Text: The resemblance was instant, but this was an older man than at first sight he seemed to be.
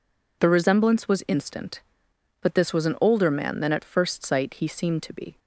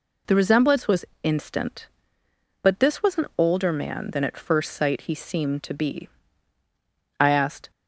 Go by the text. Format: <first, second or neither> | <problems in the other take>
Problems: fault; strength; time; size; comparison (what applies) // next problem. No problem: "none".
first | pauses between "was" and "instant"; slight; at 1.0 s; 0.18 s long // goes on to say "I asked"; from 7.2 s on; 0.50 s long